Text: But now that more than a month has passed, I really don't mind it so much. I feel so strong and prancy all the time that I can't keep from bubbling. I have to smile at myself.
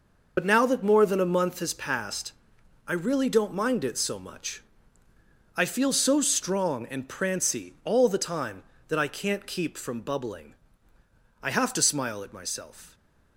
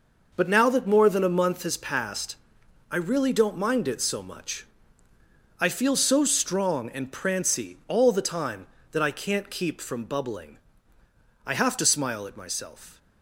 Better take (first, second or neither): second